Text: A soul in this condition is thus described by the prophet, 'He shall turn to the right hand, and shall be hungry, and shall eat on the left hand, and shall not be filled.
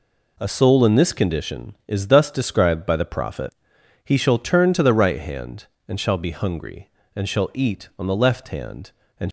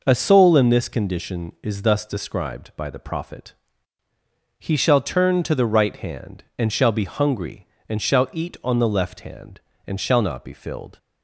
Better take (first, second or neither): second